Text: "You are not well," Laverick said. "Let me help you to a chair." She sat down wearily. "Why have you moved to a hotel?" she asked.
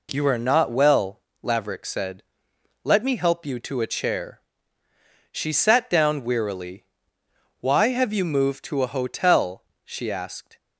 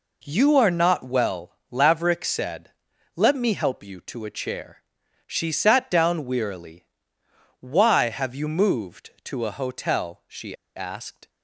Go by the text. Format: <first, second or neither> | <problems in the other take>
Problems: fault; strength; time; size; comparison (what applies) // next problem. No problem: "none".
first | pauses between "she" and "asked"; slight; at 10.5 s; 0.21 s long